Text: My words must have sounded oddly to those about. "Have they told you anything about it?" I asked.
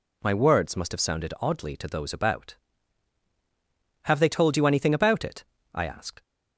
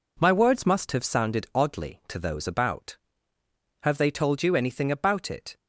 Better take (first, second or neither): first